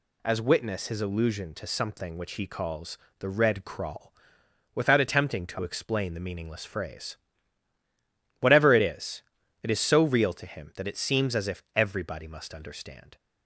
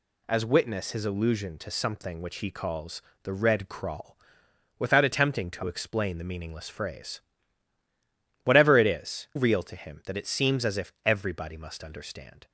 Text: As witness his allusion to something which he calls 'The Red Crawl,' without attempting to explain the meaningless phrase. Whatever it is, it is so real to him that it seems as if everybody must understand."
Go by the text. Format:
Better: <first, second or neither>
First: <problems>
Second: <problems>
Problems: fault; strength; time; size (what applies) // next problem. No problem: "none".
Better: first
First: pauses between "calls" and "The"; slight; at 2.9 s; 0.22 s long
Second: pauses between "calls" and "The"; slight; at 3.0 s; 0.22 s long // skips "it is so"; at 9.3 s